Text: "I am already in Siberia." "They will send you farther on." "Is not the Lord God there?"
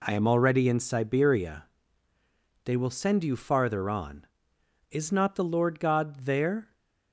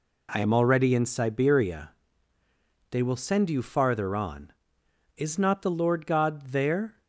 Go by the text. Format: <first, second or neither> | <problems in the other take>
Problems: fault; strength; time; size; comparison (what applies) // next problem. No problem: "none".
neither | none